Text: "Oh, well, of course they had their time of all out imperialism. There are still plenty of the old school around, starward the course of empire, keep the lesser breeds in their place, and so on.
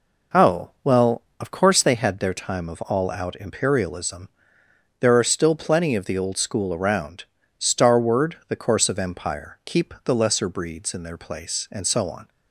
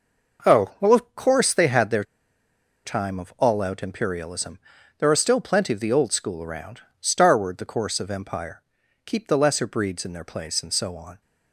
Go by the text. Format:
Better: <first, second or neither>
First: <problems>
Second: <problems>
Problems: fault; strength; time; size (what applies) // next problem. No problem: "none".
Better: first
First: none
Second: pauses between "their" and "time"; noticeable; at 2.0 s; 0.82 s long